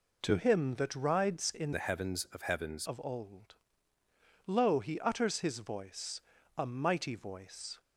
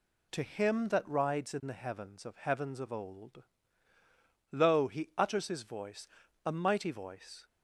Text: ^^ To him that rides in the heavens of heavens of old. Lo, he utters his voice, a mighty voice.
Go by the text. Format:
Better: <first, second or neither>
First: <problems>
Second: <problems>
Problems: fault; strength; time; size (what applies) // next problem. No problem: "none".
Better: second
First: changes voice from "the" to "heavens"; from 1.7 to 2.8 s; 1.1 s long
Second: none